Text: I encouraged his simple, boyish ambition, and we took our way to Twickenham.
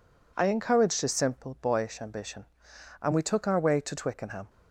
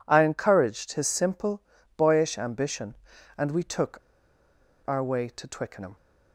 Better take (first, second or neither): first